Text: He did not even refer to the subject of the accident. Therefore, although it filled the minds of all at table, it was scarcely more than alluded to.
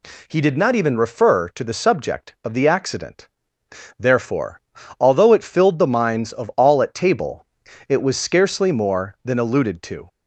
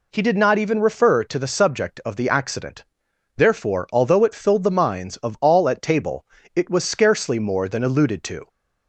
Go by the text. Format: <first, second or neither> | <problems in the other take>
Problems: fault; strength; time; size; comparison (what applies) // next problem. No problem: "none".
neither | none